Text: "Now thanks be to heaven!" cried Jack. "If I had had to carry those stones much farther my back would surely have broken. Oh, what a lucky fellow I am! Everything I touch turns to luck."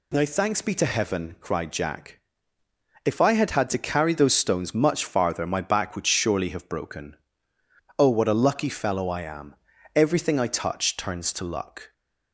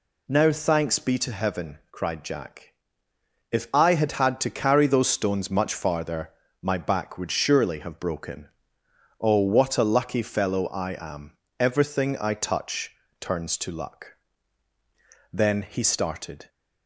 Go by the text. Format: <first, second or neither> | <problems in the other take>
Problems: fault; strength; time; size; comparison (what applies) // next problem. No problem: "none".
first | pauses between "farther" and "my"; slight; at 6.3 s; 0.32 s long // pauses between "touch" and "turns"; slight; at 12.9 s; 0.26 s long // goes on to say "Then he started"; noticeable; from 15.3 s on; 1.1 s long